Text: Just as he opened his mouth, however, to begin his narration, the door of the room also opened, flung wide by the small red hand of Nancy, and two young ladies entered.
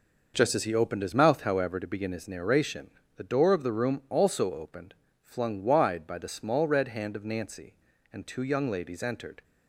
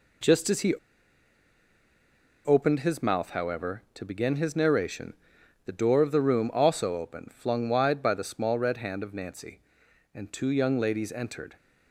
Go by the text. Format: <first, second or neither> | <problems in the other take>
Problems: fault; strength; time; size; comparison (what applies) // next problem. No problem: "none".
first | pauses between "he" and "opened"; strong; at 0.7 s; 1.7 s long